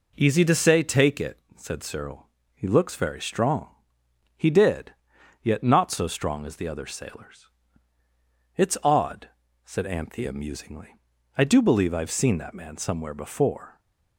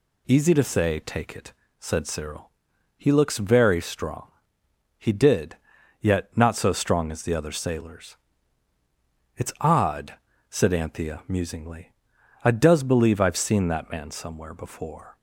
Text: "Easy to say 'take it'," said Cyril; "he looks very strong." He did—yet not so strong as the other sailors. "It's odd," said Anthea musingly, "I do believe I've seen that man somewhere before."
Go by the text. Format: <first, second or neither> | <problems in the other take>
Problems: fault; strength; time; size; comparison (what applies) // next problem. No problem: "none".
first | says "does" for "do"; at 12.5 s